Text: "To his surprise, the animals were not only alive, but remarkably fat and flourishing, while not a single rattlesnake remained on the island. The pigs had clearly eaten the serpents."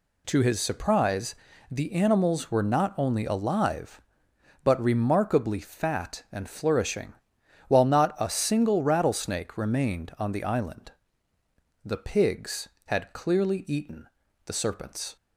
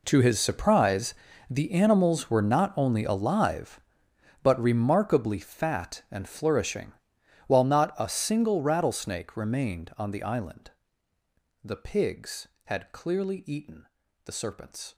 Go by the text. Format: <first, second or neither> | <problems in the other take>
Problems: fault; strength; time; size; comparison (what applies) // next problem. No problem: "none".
first | gets quieter; strong; throughout; 16 dB // pauses between "eaten" and "the"; at 13.8 s; 0.38 s long; also in the first